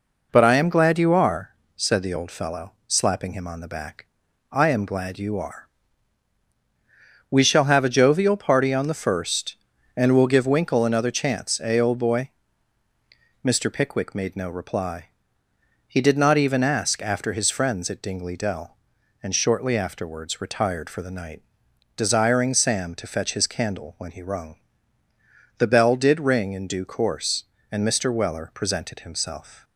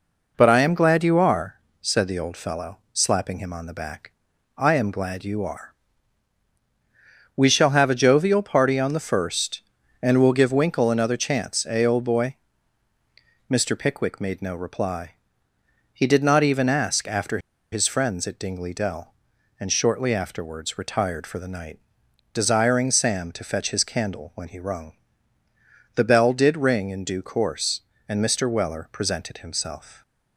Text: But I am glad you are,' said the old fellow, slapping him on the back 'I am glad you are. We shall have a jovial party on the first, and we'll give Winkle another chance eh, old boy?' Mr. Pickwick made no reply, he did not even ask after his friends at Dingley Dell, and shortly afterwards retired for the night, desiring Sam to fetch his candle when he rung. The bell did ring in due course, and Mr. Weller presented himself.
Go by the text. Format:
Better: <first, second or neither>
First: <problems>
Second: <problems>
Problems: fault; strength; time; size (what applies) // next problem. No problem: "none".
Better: first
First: pauses between "back" and "I"; noticeable; at 4.0 s; 0.46 s long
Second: pauses between "back" and "I"; noticeable; at 4.1 s; 0.46 s long // pauses between "after" and "his"; slight; at 17.3 s; 0.33 s long